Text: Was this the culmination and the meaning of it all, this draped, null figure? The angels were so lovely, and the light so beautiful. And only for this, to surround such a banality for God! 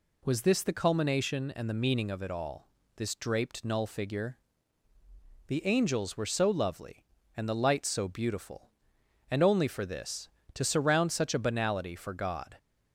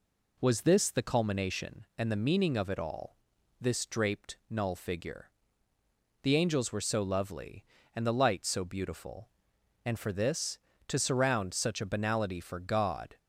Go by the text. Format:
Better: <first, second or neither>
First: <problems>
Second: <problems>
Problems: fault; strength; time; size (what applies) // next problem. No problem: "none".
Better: first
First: none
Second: skips "only"; at 9.9 s